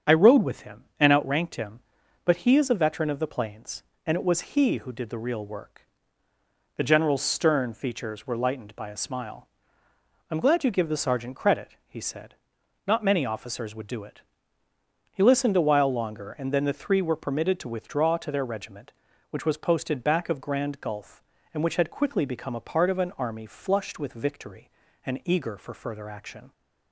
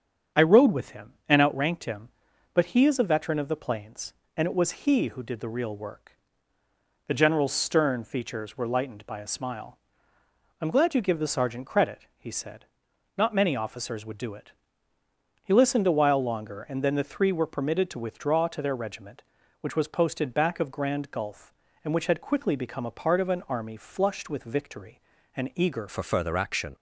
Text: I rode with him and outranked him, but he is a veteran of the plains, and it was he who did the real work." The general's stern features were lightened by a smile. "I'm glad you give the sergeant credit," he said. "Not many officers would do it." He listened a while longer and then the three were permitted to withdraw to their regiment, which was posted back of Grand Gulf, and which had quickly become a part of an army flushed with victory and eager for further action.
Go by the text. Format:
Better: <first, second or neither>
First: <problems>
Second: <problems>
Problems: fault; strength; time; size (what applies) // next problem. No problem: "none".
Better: first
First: starts louder than the rest; strong; until 1.2 s; 7.5 dB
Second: starts louder than the rest; strong; until 1.5 s; 7.5 dB // changes voice at "for"; from 25.8 s on; 0.9 s long